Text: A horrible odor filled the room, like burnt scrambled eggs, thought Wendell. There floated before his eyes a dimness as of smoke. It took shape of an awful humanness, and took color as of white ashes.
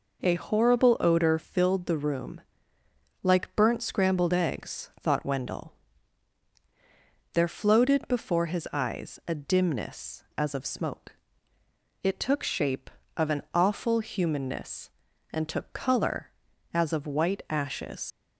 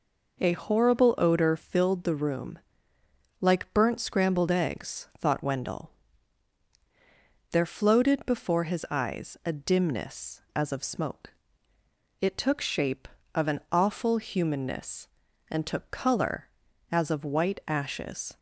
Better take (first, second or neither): second